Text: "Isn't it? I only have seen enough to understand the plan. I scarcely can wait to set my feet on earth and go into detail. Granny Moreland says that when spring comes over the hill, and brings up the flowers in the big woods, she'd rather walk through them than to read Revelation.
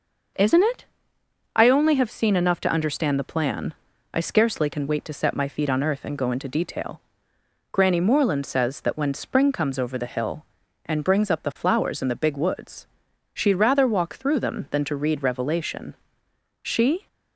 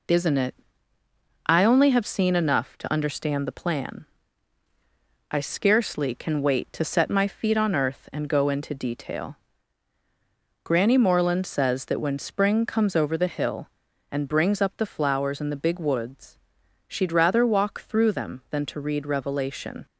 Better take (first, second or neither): second